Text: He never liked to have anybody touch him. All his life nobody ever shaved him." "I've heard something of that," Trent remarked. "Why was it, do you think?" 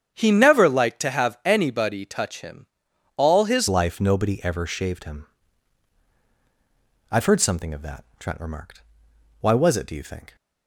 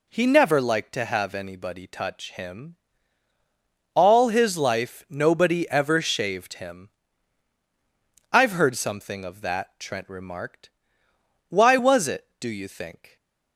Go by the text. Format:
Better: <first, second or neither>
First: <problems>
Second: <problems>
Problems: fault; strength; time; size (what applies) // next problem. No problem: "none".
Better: second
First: starts louder than the rest; strong; until 1.1 s; 8 dB // changes voice at "life"; from 3.6 s on; 6.7 s long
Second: none